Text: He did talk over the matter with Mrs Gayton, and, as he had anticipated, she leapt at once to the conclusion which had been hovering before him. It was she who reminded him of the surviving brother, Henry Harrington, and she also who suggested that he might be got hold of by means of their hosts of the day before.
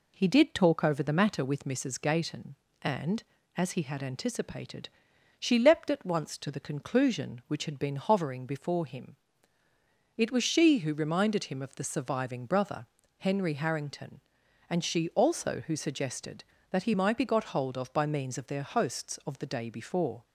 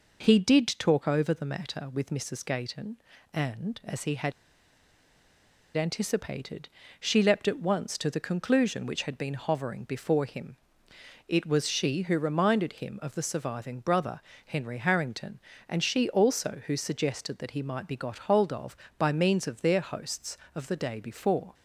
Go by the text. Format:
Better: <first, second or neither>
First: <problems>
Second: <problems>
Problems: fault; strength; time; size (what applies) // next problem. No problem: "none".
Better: first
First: none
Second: pauses between "had" and "anticipated"; strong; at 4.3 s; 1.4 s long